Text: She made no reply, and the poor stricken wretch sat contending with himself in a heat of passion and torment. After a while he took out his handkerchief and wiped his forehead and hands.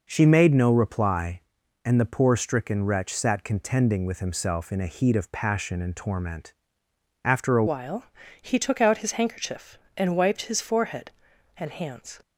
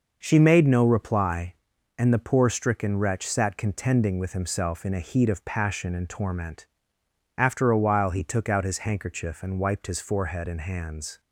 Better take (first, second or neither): second